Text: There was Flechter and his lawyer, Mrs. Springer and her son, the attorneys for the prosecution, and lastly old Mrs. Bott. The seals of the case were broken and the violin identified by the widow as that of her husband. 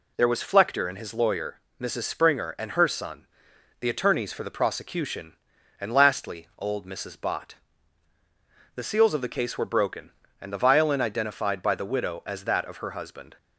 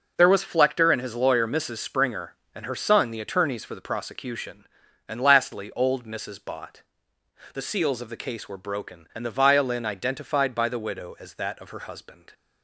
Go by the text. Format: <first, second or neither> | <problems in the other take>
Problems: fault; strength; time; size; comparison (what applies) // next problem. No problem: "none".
neither | none